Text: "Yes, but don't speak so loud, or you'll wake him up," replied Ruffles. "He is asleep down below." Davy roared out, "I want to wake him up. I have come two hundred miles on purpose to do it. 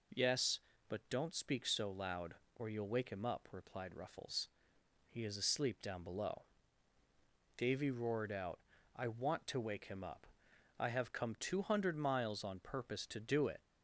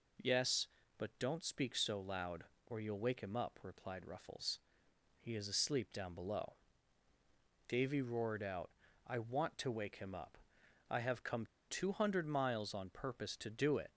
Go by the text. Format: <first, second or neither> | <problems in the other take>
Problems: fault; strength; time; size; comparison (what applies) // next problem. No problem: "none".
first | pauses between "come" and "two"; slight; at 11.4 s; 0.24 s long